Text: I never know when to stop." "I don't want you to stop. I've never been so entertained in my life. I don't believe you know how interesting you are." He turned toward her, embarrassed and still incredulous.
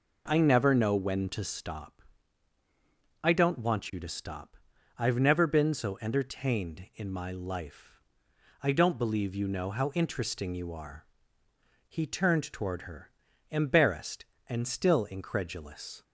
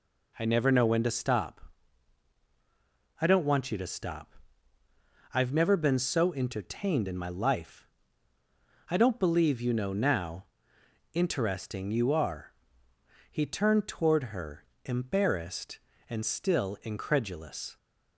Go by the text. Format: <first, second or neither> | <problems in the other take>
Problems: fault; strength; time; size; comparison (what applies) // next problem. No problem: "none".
first | says "now" for "how"; at 9.9 s